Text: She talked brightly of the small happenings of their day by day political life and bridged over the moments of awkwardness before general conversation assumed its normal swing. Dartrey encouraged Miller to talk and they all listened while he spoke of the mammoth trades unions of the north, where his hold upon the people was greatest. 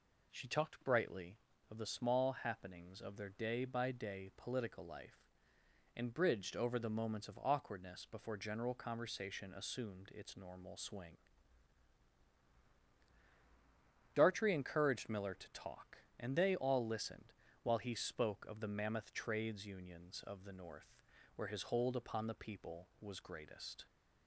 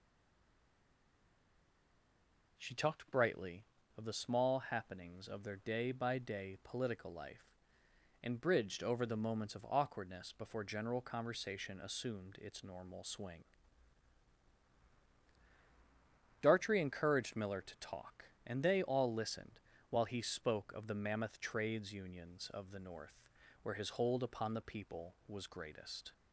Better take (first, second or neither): first